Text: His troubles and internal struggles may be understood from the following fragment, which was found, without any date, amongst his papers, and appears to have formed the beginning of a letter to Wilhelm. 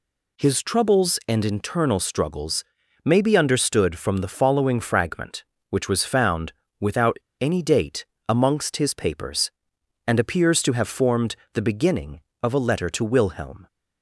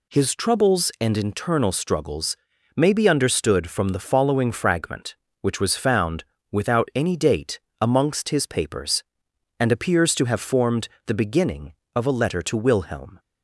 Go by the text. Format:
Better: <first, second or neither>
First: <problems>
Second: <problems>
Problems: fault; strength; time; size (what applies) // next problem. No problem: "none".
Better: second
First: pauses between "struggles" and "may"; at 2.6 s; 0.40 s long // pauses between "without" and "any"; slight; at 7.1 s; 0.25 s long // pauses between "formed" and "the"; slight; at 11.3 s; 0.20 s long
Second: pauses between "struggles" and "may"; at 2.3 s; 0.39 s long // pauses between "formed" and "the"; slight; at 10.8 s; 0.20 s long